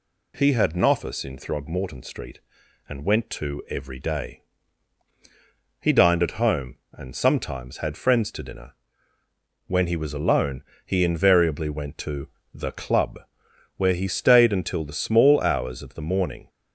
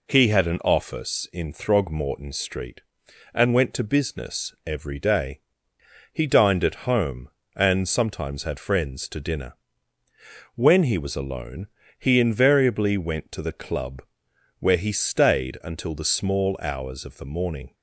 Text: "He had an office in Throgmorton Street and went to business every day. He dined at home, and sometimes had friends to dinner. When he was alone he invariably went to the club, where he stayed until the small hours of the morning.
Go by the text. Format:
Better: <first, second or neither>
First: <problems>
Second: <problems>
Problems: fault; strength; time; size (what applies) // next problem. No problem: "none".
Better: second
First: skips "business"; at 3.6 s // pauses between "alone" and "he"; slight; at 10.6 s; 0.22 s long // pauses between "to" and "the"; slight; at 12.2 s; 0.26 s long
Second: pauses between "alone" and "he"; slight; at 11.6 s; 0.32 s long